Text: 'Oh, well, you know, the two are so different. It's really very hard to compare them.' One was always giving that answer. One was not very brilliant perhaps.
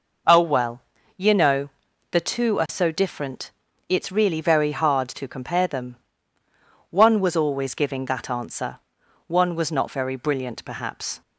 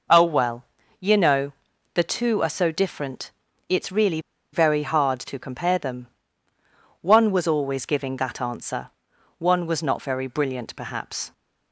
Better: first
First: none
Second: pauses between "really" and "very"; slight; at 4.1 s; 0.33 s long

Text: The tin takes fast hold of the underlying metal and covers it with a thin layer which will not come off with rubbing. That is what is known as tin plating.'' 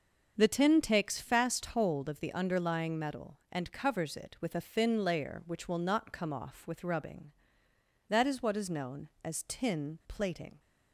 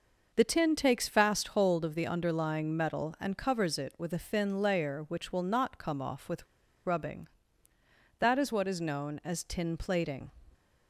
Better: first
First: starts louder than the rest; until 1.3 s; 6.5 dB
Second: starts louder than the rest; noticeable; until 1.3 s; 6 dB // pauses between "with" and "rubbing"; at 6.4 s; 0.40 s long

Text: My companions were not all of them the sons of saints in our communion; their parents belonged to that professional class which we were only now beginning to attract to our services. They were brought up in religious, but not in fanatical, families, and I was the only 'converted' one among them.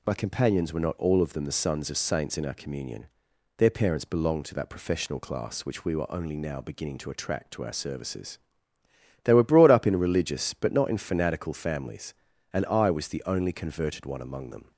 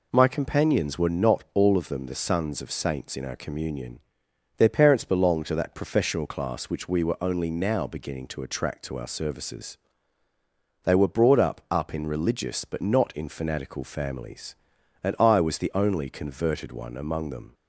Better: first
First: none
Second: says "up" twice; at 11.6 s

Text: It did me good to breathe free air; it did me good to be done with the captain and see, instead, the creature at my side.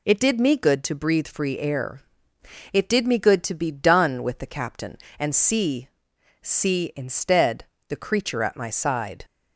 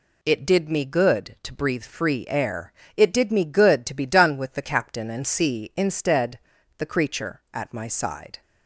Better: second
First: says "see" twice; at 6.4 s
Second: none

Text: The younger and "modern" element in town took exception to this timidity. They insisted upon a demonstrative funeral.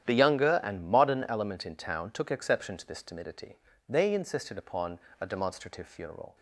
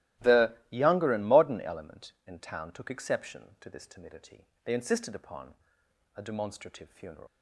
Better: first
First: starts louder than the rest; strong; until 1.1 s; 10.5 dB // pauses between "upon" and "a"; slight; at 4.9 s; 0.22 s long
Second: starts louder than the rest; strong; until 1.3 s; 15.5 dB // pauses between "The" and "younger"; slight; at 0.5 s; 0.16 s long // pauses between "upon" and "a"; noticeable; at 5.5 s; 0.62 s long // leaves "funeral" unfinished; at 7.2 s; 110 ms

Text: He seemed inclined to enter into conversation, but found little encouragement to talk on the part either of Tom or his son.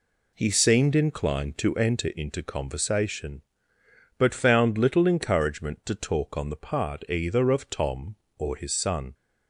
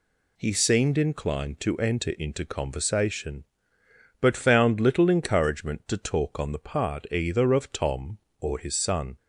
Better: second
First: starts louder than the rest; slight; until 2.1 s; 2.5 dB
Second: none

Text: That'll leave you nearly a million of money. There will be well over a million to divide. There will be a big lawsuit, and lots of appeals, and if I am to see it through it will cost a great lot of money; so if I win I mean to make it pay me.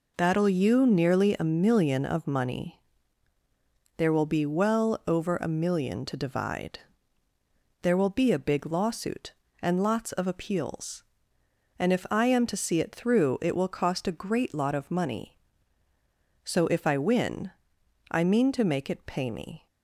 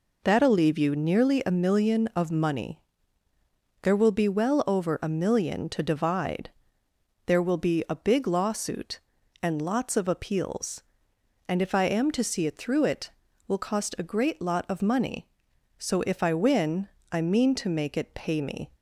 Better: second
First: skips "leave"; at 0.4 s // pauses between "win" and "I"; noticeable; at 17.5 s; 0.62 s long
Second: pauses between "win" and "I"; slight; at 16.8 s; 0.22 s long

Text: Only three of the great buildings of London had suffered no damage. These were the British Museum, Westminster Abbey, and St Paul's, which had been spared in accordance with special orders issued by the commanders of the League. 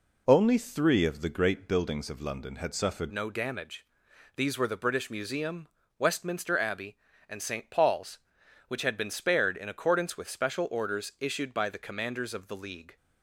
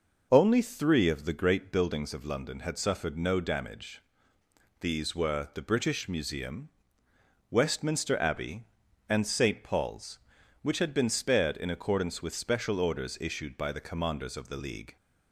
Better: second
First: changes voice at "no"; from 3.1 s on; 9.8 s long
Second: none

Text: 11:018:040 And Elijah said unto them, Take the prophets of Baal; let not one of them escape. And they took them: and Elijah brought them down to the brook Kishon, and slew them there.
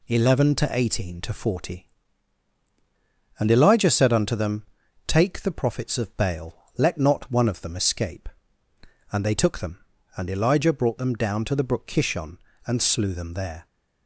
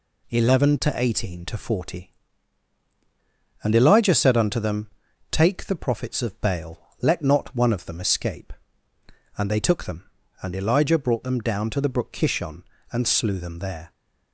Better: neither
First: none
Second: none

